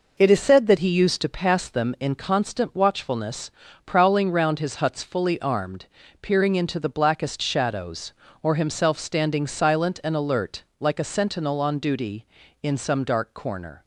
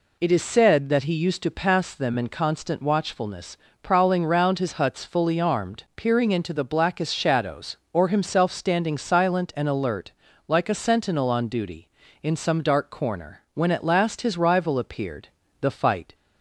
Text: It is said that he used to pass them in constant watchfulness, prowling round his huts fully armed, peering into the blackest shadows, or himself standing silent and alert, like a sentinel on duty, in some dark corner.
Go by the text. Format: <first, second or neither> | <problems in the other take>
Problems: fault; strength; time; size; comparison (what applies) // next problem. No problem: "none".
first | goes on to say "When at last his rival appeared the fight"; strong; from 13.5 s on; 2.6 s long